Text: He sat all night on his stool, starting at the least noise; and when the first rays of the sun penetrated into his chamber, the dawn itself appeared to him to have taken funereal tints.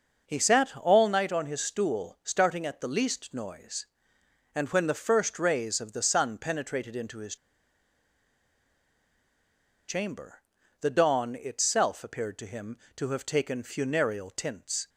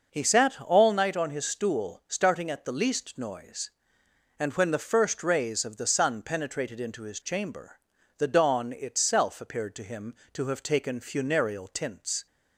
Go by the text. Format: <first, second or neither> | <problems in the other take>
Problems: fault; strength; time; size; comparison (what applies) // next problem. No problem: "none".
second | pauses between "his" and "chamber"; strong; at 7.3 s; 2.5 s long